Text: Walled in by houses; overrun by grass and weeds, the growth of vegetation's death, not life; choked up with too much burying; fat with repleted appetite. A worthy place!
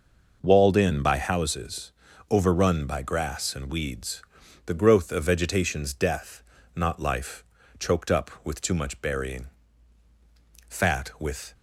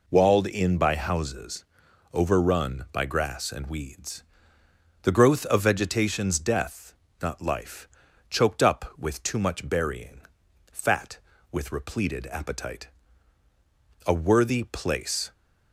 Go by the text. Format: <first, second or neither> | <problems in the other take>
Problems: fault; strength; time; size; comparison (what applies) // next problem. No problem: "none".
second | stops before "repleted appetite A worthy place"; at 11.5 s